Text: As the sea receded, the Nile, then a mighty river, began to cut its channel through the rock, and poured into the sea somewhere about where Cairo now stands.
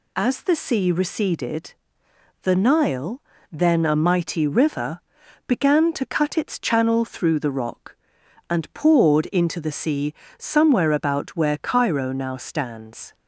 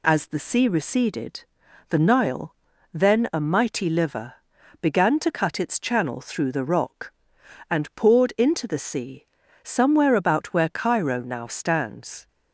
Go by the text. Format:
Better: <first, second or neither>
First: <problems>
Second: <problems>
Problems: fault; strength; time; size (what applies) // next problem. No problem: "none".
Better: first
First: pauses between "sea" and "somewhere"; slight; at 10.1 s; 0.24 s long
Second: says "liver" for "river"; at 3.8 s // pauses between "sea" and "somewhere"; at 9.2 s; 0.38 s long